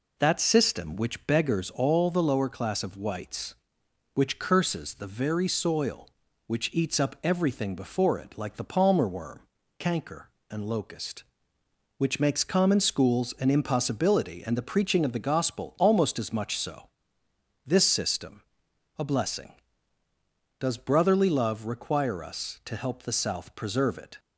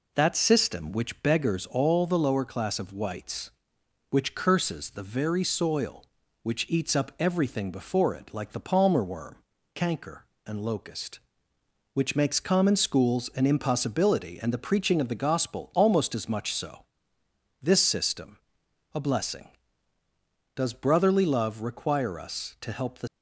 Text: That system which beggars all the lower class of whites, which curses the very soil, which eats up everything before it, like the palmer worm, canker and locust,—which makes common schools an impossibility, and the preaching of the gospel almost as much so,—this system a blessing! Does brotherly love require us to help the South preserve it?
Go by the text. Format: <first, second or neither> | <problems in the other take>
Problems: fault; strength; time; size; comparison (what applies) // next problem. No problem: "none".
first | pauses between "system" and "a"; noticeable; at 18.3 s; 0.56 s long; noticeable in the first // stops before "South preserve it"; at 23.0 s